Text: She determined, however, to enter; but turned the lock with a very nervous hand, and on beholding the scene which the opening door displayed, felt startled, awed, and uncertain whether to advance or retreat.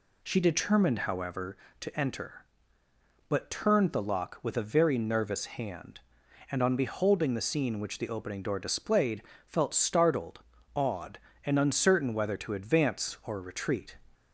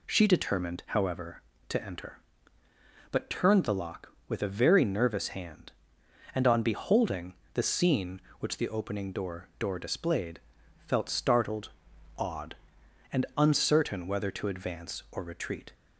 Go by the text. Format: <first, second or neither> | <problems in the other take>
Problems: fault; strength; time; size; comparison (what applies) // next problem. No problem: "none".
first | pauses between "beholding" and "the"; slight; at 7.3 s; 0.22 s long // says "door" twice; at 9.5 s